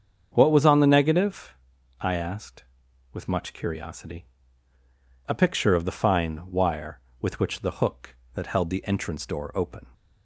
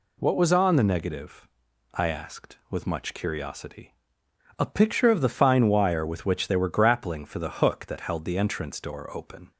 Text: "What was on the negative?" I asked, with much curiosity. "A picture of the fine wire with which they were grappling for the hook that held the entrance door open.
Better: second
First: starts louder than the rest; until 1.3 s; 7 dB // skips "they were grappling for"; at 7.6 s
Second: none

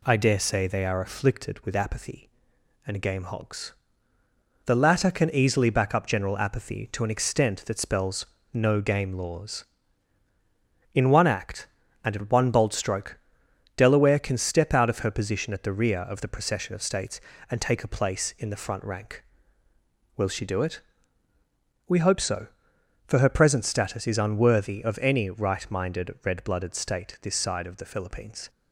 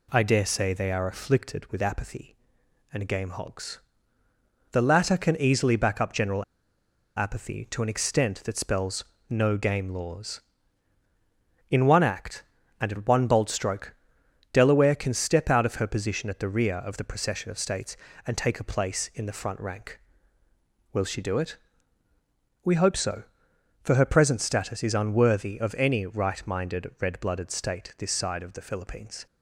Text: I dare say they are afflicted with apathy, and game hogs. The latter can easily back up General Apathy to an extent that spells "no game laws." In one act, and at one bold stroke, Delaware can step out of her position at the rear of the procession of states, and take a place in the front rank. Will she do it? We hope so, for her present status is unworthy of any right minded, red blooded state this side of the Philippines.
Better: first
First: pauses between "spells" and "no"; slight; at 8.2 s; 0.28 s long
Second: pauses between "General" and "Apathy"; noticeable; at 6.4 s; 0.72 s long // pauses between "spells" and "no"; slight; at 9.0 s; 0.26 s long

